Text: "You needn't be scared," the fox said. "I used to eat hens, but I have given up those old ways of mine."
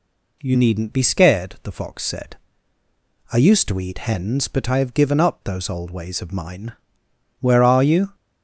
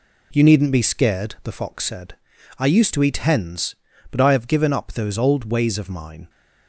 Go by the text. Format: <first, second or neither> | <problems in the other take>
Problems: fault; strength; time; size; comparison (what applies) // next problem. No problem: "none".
second | goes on to say "Where are you"; noticeable; from 7.3 s on; 0.76 s long